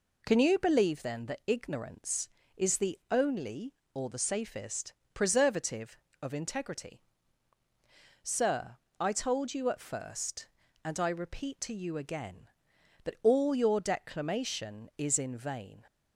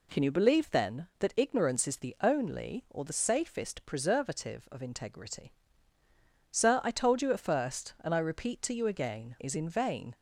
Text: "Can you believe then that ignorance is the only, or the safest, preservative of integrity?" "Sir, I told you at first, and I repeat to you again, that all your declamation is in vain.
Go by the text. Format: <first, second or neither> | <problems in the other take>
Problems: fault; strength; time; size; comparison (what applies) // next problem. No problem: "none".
first | skips "that all your declamation"; at 9.3 s